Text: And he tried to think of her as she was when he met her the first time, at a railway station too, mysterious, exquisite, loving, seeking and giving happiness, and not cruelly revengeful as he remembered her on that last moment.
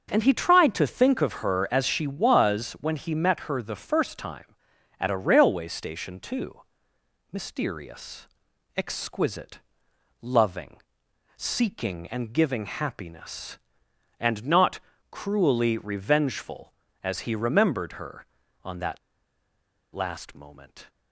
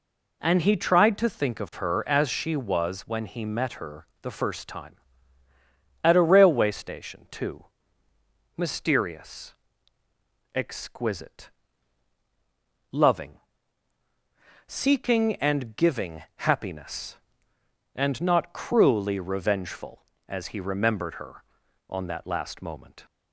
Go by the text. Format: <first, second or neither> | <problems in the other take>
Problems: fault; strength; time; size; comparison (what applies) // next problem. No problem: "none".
second | starts louder than the rest; until 1.1 s; 6.5 dB // pauses between "not" and "cruelly"; slight; at 14.7 s; 0.32 s long // pauses between "that" and "last"; noticeable; at 18.9 s; 0.94 s long